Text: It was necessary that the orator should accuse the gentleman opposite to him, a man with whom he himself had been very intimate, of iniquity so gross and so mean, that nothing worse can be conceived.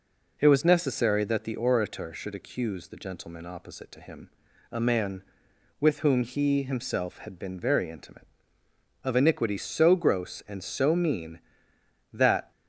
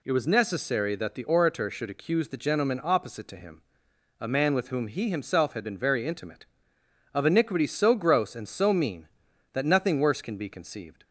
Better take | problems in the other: second | stops before "nothing worse can be conceived"; at 12.5 s

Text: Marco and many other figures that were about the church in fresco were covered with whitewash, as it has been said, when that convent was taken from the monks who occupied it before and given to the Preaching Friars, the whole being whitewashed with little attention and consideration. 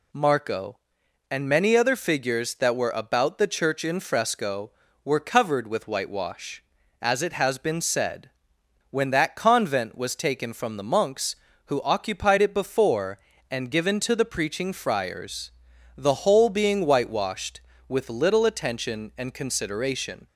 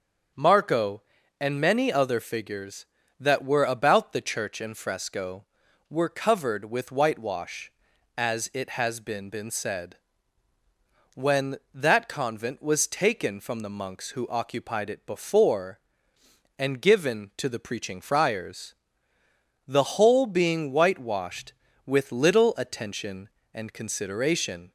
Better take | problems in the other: first | starts louder than the rest; until 1.7 s; 7 dB // says "been" twice; at 9.2 s

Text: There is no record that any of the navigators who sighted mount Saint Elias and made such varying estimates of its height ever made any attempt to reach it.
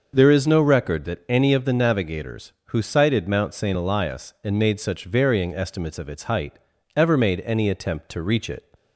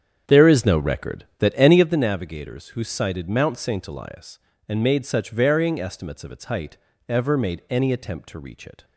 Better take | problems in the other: first | starts louder than the rest; strong; until 2.0 s; 8 dB // pauses between "height" and "ever"; slight; at 6.7 s; 0.32 s long; slight in the first

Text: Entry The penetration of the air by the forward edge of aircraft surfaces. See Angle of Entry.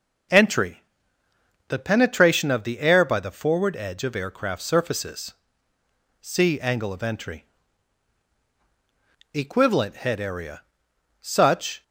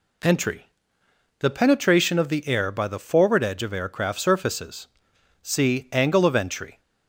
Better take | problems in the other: second | pauses between "Entry" and "The"; noticeable; at 0.8 s; 0.86 s long; noticeable in the second // goes on to say "Equivalent Head Area Such"; strong; from 9.3 s on; 2.4 s long

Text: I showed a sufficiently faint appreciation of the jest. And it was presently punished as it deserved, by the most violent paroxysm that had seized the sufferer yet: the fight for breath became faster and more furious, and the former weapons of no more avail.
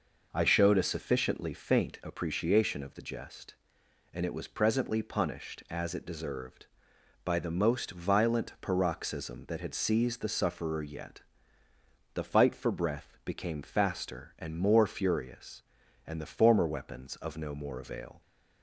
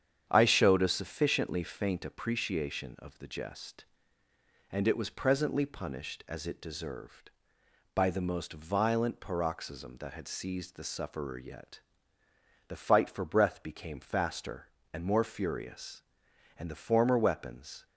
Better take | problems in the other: first | starts louder than the rest; strong; until 1.3 s; 8.5 dB // stops before "of no more avail"; at 17.8 s

